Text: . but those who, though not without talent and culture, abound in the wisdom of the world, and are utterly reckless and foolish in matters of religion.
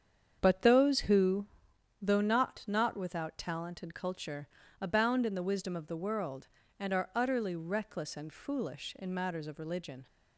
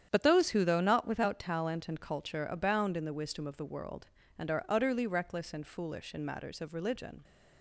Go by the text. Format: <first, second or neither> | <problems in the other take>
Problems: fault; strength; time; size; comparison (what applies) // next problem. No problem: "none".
second | starts louder than the rest; strong; until 1.4 s; 8 dB; strong in the second // says "not" twice; at 2.6 s